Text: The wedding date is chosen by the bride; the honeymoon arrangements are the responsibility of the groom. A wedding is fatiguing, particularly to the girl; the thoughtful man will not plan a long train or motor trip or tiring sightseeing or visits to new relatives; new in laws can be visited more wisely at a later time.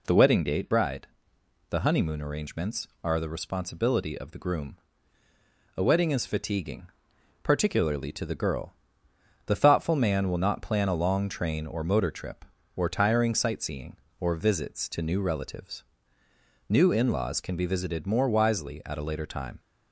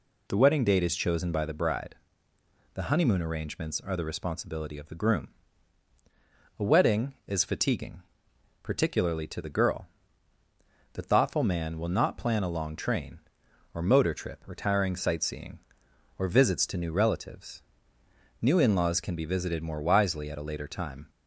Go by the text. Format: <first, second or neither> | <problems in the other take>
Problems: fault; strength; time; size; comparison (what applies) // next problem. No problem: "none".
second | skips "is chosen by the"; at 0.6 s